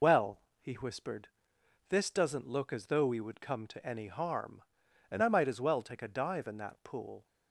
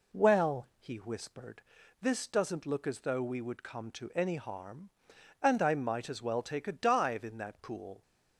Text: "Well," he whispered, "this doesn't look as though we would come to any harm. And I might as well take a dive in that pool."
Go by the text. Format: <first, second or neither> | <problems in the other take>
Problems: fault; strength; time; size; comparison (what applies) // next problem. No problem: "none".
second | loses the start of "Well"; at 0.0 s; 75 ms